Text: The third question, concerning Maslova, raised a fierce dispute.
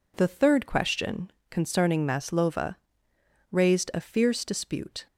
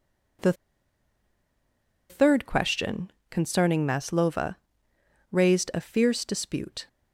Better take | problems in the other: first | pauses between "The" and "third"; strong; at 0.5 s; 1.5 s long

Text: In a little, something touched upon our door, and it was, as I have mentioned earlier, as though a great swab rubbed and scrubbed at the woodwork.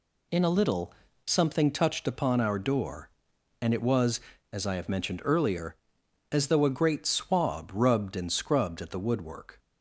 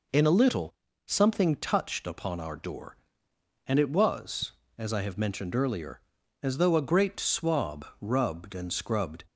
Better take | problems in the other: first | pauses between "swab" and "rubbed"; slight; at 7.8 s; 0.16 s long // stops before "at the woodwork"; at 9.2 s

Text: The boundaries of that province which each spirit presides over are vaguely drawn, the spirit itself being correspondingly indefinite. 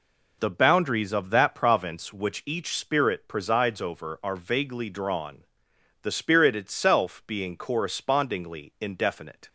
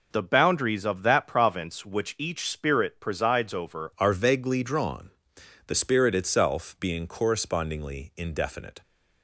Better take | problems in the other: first | changes voice at "are"; from 3.9 s on; 4.9 s long

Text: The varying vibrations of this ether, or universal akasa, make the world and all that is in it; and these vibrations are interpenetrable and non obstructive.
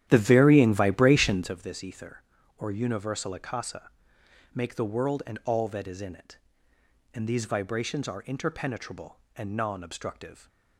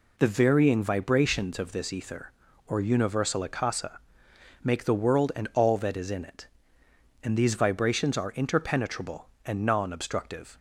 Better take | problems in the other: second | starts louder than the rest; strong; until 1.5 s; 11.5 dB

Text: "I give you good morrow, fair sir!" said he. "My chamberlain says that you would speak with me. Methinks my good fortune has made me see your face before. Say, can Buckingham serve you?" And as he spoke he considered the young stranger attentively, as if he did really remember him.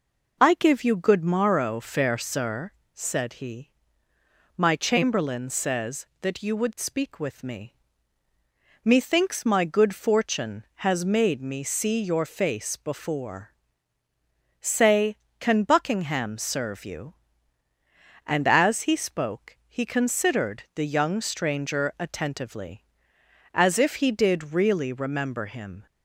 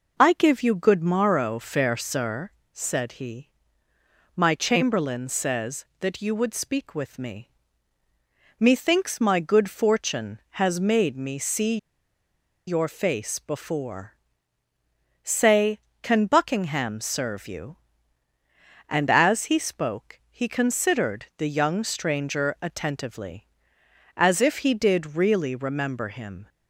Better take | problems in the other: first | pauses between "see" and "your"; noticeable; at 11.7 s; 0.90 s long

